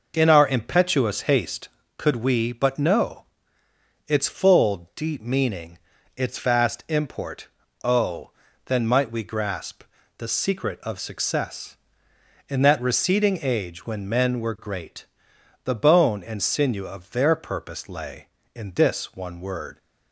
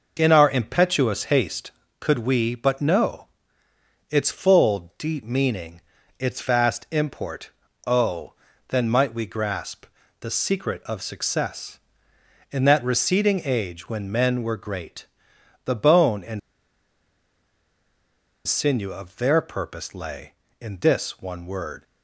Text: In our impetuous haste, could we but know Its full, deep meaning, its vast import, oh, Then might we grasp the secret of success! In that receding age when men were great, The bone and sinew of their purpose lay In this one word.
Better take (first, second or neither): first